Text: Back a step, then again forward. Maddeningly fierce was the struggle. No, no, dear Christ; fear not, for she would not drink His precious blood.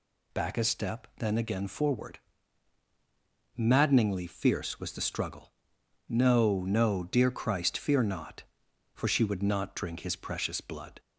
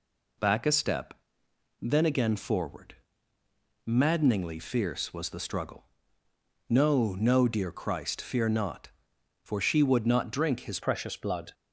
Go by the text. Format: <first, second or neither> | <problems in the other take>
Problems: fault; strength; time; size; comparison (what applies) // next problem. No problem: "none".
first | changes voice at "precious"; from 10.8 s on; 0.7 s long